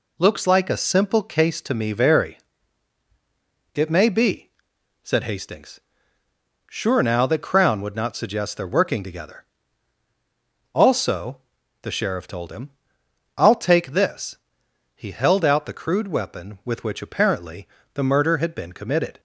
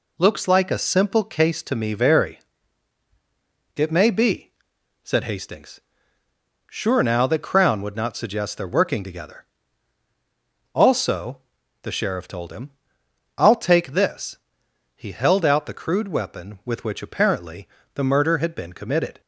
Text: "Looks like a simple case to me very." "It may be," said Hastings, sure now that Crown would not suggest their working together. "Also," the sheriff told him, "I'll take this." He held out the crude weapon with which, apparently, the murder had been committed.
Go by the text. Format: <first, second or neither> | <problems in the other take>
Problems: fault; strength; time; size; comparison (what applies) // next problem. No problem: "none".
neither | none